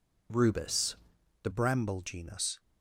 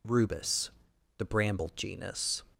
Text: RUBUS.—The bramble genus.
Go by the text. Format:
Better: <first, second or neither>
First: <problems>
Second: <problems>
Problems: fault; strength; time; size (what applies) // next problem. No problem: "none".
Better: second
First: changes voice at "bramble"; from 1.5 s on; 1.0 s long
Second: none